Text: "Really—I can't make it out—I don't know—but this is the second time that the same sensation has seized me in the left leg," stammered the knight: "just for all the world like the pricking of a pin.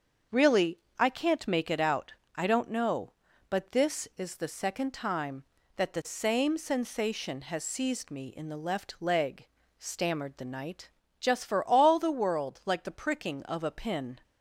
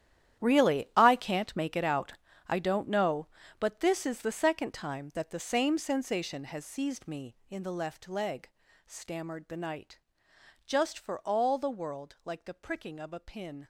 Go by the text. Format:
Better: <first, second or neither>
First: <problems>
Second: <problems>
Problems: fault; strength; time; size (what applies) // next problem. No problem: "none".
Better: first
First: starts louder than the rest; until 1.5 s; 7 dB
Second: gets quieter; strong; throughout; 15 dB // starts louder than the rest; strong; until 1.4 s; 11 dB